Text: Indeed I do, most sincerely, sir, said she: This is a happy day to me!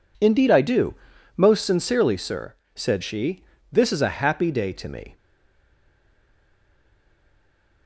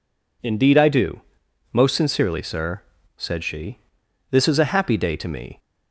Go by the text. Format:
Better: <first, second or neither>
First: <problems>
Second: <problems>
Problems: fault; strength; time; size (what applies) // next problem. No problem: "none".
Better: second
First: stays silent after the last word; strong; from 5.1 s on; 2.7 s long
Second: none